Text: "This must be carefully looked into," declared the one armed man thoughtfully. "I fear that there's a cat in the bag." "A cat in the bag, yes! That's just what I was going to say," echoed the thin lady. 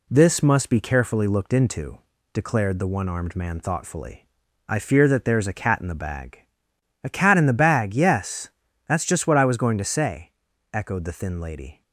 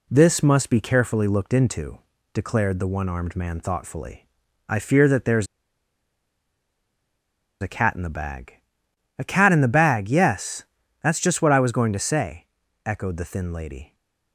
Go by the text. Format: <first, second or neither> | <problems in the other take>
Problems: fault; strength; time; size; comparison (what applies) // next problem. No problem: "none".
first | pauses between "there's" and "a"; strong; at 5.4 s; 2.1 s long